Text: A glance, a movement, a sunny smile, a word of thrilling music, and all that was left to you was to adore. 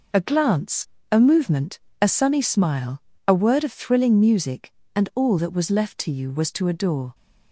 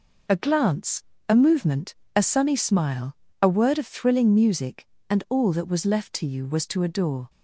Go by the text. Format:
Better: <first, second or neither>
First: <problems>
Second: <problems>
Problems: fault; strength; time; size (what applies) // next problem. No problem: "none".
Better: neither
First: none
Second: none